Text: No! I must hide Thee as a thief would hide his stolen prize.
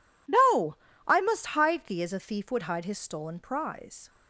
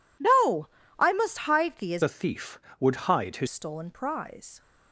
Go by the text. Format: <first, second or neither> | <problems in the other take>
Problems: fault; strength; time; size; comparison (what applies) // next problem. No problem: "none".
first | changes voice from "a" to "his"; from 2.0 to 3.4 s; 1.4 s long